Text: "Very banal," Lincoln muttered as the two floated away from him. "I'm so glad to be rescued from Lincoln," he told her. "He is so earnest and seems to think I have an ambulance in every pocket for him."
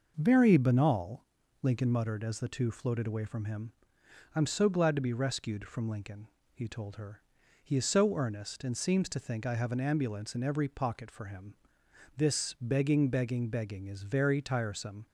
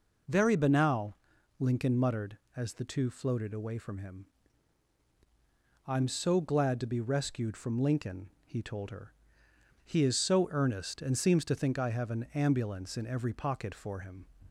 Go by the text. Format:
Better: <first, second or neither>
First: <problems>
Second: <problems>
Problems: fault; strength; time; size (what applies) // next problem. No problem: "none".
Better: second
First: goes on to say "This begging begging begging is very tiresome"; strong; from 12.1 s on; 2.8 s long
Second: none